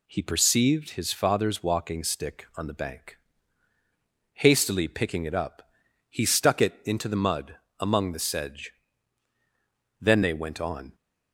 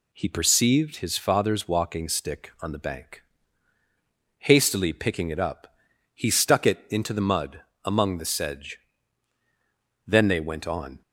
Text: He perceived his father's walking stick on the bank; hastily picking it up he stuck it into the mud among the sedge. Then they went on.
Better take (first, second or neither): neither